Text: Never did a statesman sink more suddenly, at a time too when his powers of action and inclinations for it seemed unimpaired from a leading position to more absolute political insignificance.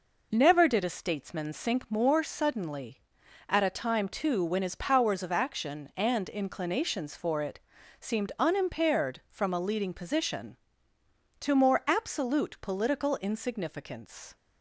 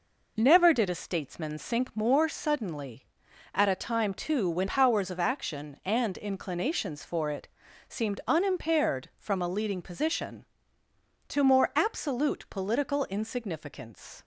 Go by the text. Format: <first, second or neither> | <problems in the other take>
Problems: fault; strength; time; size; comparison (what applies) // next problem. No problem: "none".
first | skips "his"; at 4.6 s // pauses between "it" and "seemed"; at 7.4 s; 0.42 s long; also in the first